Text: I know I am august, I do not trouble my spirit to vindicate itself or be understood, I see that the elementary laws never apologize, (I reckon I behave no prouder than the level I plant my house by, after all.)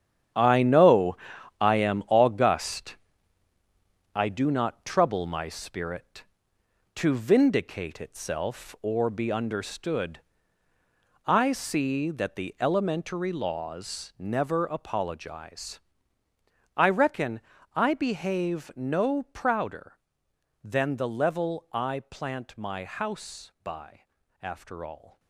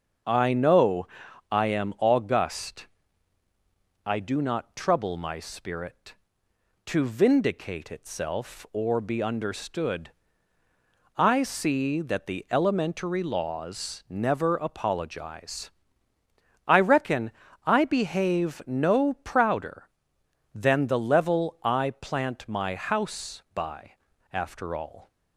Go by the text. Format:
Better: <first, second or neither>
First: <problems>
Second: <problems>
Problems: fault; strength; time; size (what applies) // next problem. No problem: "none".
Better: second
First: gets quieter; strong; throughout; 9.5 dB // starts louder than the rest; strong; until 1.8 s; 9.5 dB // pauses between "know" and "I"; at 1.1 s; 0.42 s long // pauses between "reckon" and "I"; slight; at 17.4 s; 0.34 s long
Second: starts louder than the rest; until 1.6 s; 6.5 dB // pauses between "know" and "I"; at 1.0 s; 0.42 s long // pauses between "reckon" and "I"; slight; at 17.3 s; 0.34 s long